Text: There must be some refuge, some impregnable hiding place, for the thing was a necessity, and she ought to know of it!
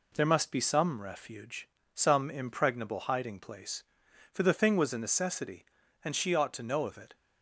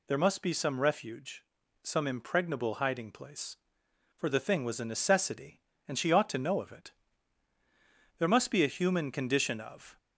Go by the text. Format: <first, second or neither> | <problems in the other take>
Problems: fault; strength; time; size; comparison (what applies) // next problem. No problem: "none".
first | goes on to say "There must be a human condition of"; strong; from 8.1 s on; 1.7 s long